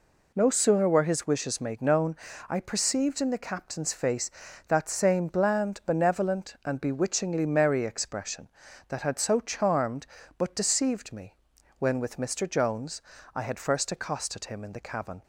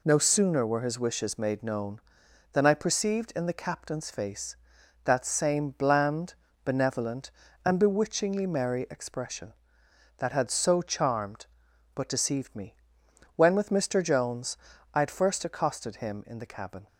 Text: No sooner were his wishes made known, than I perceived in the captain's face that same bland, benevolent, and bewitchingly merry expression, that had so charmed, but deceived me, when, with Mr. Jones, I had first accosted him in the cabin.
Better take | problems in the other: second | skips "than"; at 2.3 s

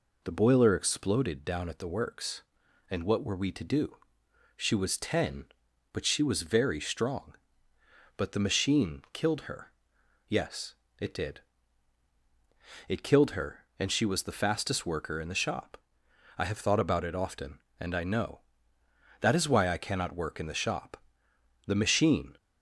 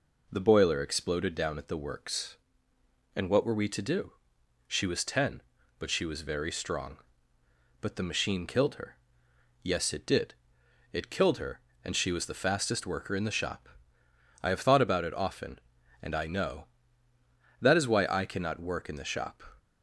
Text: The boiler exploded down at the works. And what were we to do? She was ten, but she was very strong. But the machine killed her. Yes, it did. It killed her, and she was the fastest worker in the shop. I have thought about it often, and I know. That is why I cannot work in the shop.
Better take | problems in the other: second | goes on to say "The machine"; noticeable; from 21.6 s on; 0.70 s long

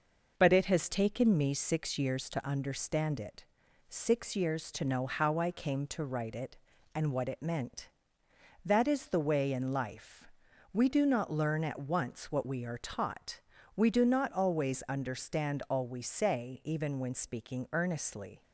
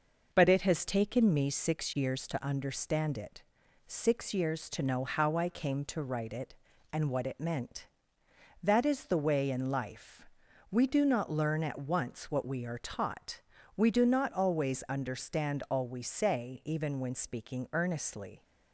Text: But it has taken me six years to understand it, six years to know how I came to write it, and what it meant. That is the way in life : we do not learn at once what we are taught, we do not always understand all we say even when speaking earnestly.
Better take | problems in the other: neither | none

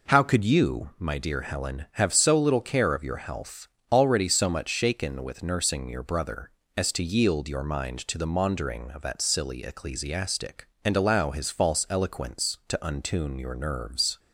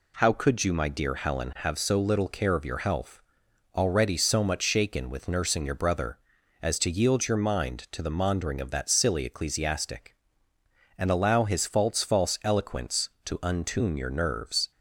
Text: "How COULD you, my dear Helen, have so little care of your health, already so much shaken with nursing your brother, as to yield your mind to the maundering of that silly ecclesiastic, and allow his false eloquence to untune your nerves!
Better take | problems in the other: first | says "false" twice; at 12.0 s

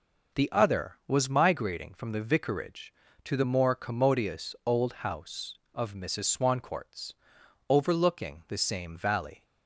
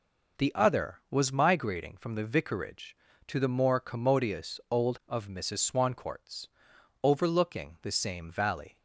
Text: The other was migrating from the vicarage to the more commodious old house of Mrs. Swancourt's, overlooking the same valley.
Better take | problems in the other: first | skips "house"; at 5.0 s

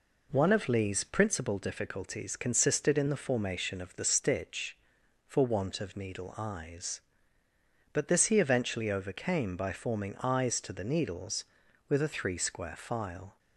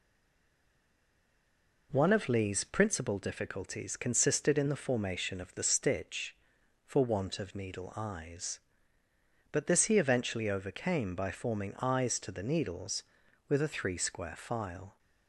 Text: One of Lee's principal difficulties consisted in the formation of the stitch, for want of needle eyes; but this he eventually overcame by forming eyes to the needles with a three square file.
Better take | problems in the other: first | stays silent before the first word; noticeable; until 1.9 s; 1.9 s long

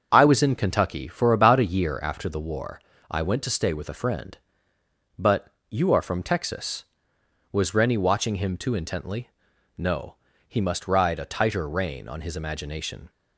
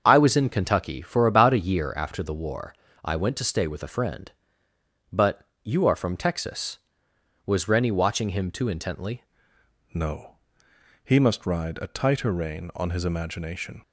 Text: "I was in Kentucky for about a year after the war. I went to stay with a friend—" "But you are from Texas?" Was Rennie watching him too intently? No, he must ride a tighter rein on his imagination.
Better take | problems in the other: first | starts louder than the rest; until 1.0 s; 6.5 dB; also in the first // pauses between "But" and "you"; slight; at 5.4 s; 0.16 s long; slight in the first // changes voice at "No"; from 9.9 s on; 3.9 s long

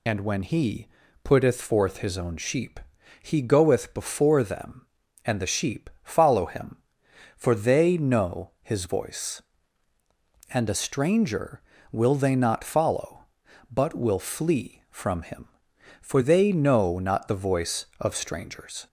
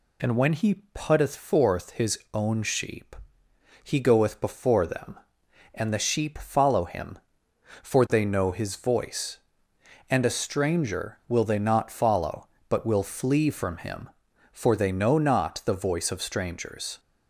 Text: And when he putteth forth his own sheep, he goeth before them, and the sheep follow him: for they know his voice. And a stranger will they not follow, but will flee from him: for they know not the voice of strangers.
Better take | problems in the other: second | loses the start of "And"; at 0.0 s; 40 ms // pauses between "he" and "putteth"; slight; at 0.8 s; 0.36 s long

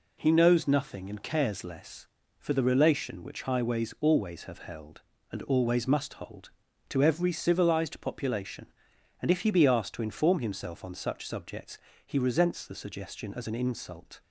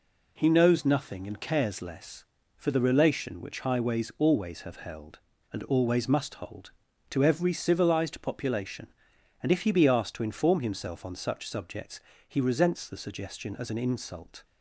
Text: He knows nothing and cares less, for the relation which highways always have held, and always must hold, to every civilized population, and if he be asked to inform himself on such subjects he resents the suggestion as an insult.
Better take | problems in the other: neither | pauses between "subjects" and "he"; slight; the same in both

